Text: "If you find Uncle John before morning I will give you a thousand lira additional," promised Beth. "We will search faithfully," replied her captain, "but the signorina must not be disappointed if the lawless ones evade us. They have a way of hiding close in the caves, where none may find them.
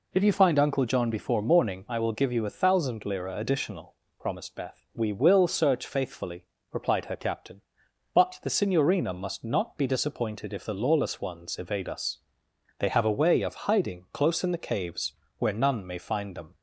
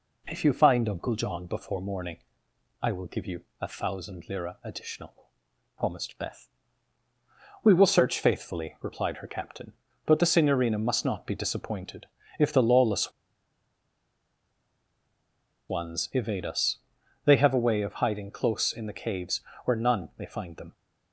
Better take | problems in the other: first | pauses between "morning" and "I"; noticeable; at 2.1 s; 0.64 s long // pauses between "you" and "a"; slight; at 3.4 s; 0.16 s long // pauses between "disappointed" and "if"; slight; at 12.0 s; 0.34 s long // pauses between "lawless" and "ones"; strong; at 13.1 s; 2.5 s long

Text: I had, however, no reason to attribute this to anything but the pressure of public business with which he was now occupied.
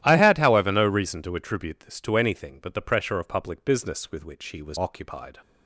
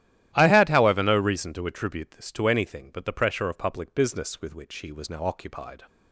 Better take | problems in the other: second | starts louder than the rest; strong; until 1.0 s; 13 dB; strong in the second // skips "now"; at 4.7 s

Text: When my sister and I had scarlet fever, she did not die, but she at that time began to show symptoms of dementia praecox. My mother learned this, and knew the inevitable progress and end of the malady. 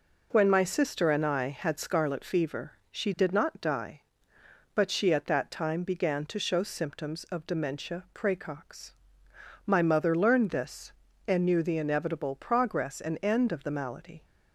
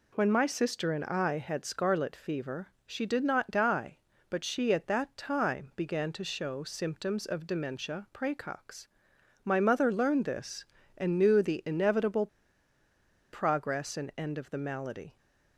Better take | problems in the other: first | pauses between "inevitable" and "progress"; at 12.2 s; 1.0 s long

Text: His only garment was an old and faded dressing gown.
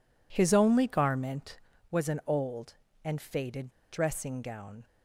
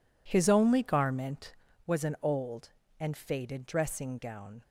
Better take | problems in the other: second | pauses between "faded" and "dressing"; slight; at 3.6 s; 0.22 s long

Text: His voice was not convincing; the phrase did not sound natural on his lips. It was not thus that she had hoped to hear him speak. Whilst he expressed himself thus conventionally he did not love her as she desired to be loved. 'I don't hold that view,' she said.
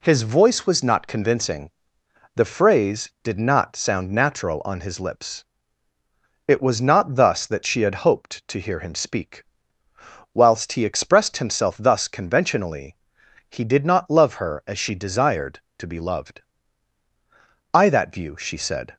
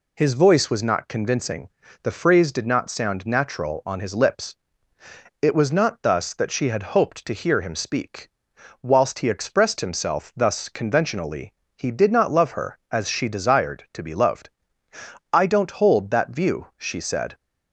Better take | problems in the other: second | pauses between "conventionally" and "he"; noticeable; at 12.9 s; 0.52 s long; slight in the second // skips "don't hold"; at 17.8 s

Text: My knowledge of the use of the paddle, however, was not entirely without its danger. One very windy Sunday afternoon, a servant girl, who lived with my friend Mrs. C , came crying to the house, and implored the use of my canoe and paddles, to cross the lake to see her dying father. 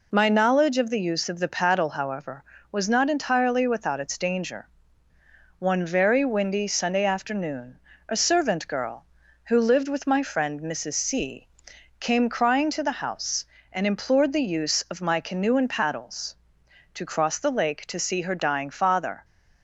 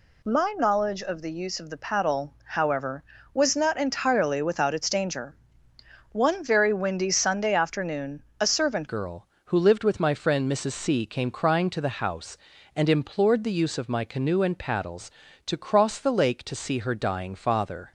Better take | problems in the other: first | changes voice at "girl"; from 8.8 s on; 9.1 s long

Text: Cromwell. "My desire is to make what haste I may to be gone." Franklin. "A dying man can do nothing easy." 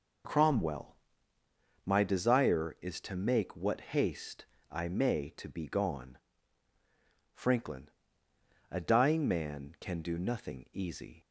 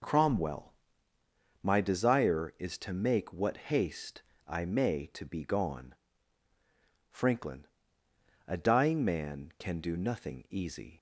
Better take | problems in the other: neither | pauses between "haste" and "I"; slight; the same in both

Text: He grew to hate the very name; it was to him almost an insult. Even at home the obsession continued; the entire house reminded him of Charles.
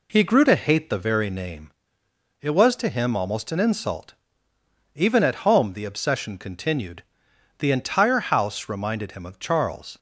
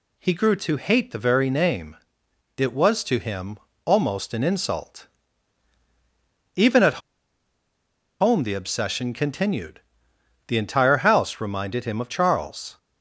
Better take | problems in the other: first | pauses between "him" and "almost"; slight; at 3.5 s; 0.28 s long // pauses between "at" and "home"; at 7.0 s; 1.2 s long

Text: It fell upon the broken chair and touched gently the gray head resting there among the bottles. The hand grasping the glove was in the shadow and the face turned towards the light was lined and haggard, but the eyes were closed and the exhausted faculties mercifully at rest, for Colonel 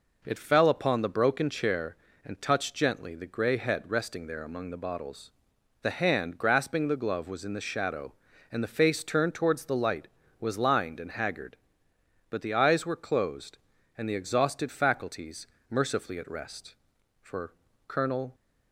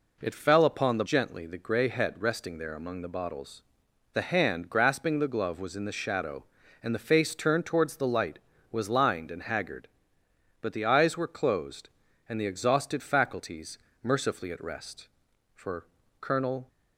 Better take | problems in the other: first | skips "broken chair and touched"; at 1.0 s // pauses between "faculties" and "mercifully"; slight; at 13.7 s; 0.24 s long; slight in the first // pauses between "for" and "Colonel"; slight; at 15.8 s; 0.34 s long; slight in the first

